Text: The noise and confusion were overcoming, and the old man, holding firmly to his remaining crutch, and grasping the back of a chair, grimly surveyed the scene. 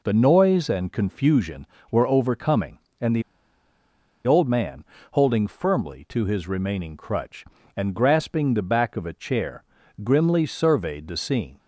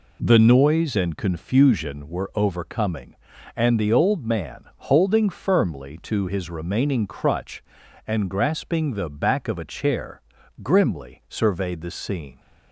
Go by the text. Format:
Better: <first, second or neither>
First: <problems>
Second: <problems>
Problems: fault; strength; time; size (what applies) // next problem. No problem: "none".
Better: second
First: pauses between "the" and "old"; at 3.2 s; 1.0 s long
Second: none